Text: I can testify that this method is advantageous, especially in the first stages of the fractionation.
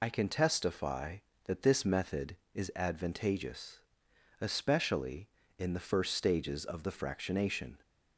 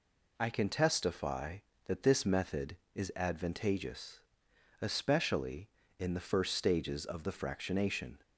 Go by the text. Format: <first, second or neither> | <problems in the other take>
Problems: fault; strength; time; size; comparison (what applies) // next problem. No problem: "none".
second | loses the start of "I"; at 0.0 s; 50 ms